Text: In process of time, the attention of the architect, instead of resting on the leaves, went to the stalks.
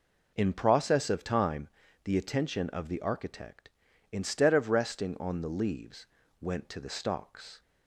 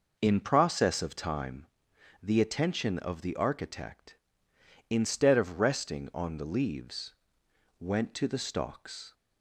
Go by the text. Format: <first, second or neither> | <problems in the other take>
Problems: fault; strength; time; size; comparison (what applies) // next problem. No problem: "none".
neither | none